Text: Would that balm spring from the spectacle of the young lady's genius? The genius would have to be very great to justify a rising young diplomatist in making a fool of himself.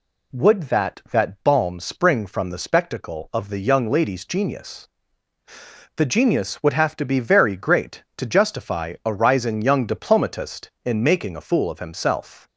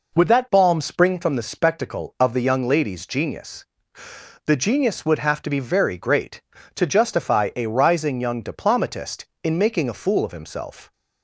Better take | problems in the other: second | says "that" twice; at 1.0 s

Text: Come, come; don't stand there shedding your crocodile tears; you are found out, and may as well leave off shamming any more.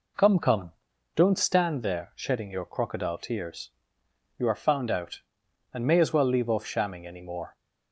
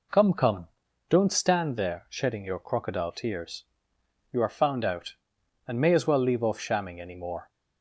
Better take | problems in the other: neither | none

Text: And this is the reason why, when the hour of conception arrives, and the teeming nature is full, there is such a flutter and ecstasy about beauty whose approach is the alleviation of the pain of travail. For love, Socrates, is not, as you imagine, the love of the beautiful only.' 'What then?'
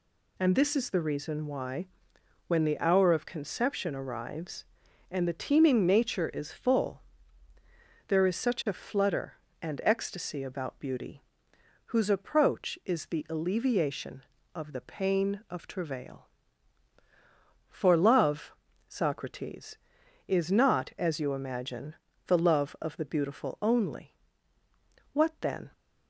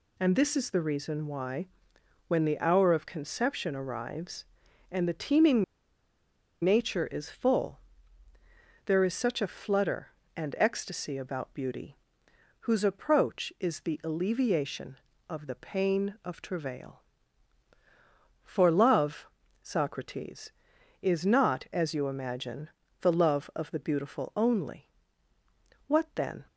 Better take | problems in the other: first | pauses between "teeming" and "nature"; at 5.6 s; 1.0 s long // pauses between "beauty" and "whose"; noticeable; at 11.9 s; 0.64 s long; noticeable in the first

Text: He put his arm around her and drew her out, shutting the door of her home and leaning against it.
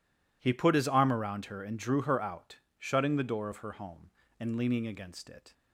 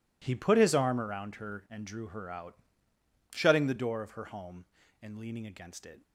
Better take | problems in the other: neither | none

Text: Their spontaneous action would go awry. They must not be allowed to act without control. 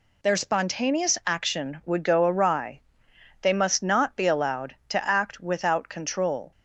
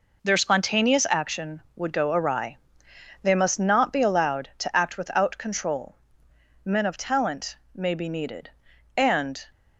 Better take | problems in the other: first | goes on to say "Men of talent may be needed and"; strong; from 6.6 s on; 2.7 s long

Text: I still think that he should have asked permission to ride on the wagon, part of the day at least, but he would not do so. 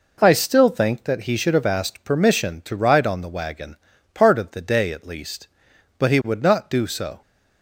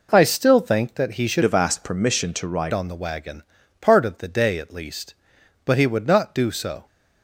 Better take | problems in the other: first | changes voice from "have" to "ride"; from 1.4 to 2.7 s; 1.3 s long

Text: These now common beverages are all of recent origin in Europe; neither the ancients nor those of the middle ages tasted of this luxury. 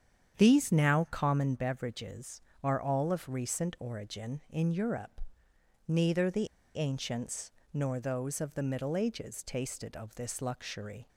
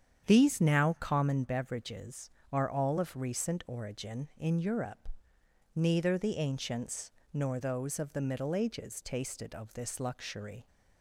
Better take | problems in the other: second | starts louder than the rest; strong; until 1.4 s; 8.5 dB; strong in the second // pauses between "the" and "ancients"; slight; at 6.4 s; 0.28 s long // pauses between "ancients" and "nor"; slight; at 7.4 s; 0.24 s long; slight in the second

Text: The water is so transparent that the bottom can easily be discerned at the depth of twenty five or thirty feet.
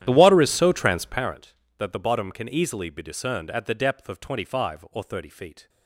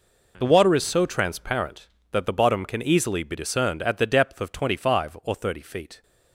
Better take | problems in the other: second | starts louder than the rest; strong; until 1.4 s; 11 dB

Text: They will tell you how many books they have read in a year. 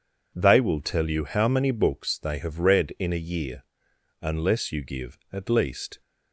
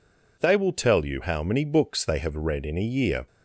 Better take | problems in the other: second | goes on to say "Unless you give at least"; strong; from 4.2 s on; 1.7 s long

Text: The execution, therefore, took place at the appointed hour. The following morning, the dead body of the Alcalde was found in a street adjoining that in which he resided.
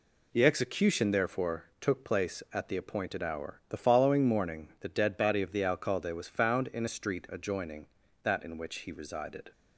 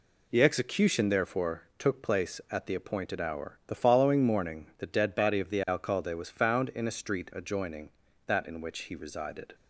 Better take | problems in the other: neither | none

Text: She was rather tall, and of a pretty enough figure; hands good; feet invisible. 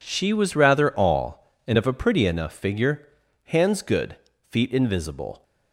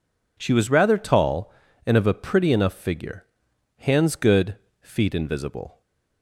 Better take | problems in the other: second | says "all" for "tall"; at 0.9 s

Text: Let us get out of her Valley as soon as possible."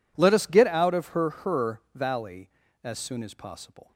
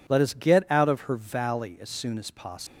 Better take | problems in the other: second | says "her" twice; at 1.2 s

